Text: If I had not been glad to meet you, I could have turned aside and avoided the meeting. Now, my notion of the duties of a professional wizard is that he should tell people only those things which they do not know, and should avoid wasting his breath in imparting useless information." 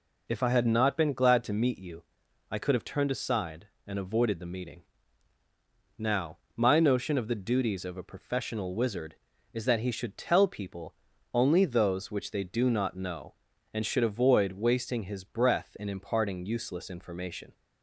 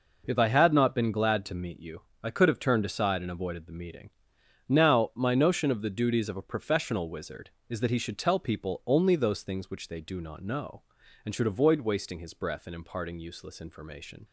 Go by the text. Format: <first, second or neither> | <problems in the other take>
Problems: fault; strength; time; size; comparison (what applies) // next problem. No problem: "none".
second | pauses between "people" and "only"; at 10.9 s; 0.38 s long // skips "things"; at 12.1 s